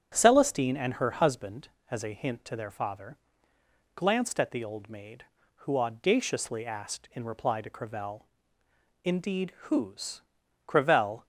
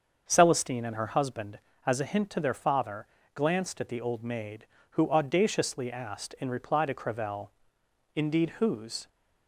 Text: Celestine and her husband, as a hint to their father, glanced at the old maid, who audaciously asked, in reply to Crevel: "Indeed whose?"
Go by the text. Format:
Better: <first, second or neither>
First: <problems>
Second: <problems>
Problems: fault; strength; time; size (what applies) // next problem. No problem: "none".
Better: second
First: starts louder than the rest; strong; until 1.1 s; 8 dB // goes on to say "Crevel"; from 10.6 s on; 0.58 s long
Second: starts louder than the rest; until 1.2 s; 6.5 dB